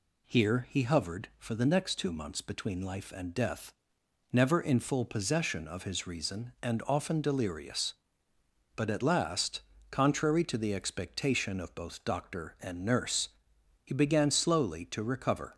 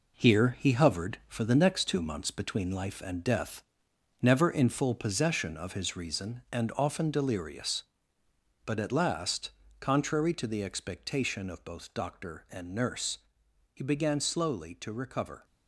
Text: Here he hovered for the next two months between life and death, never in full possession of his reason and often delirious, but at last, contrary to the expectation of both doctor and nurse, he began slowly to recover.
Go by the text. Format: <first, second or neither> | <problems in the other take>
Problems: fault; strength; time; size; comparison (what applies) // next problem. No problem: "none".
first | gets quieter; throughout; 7 dB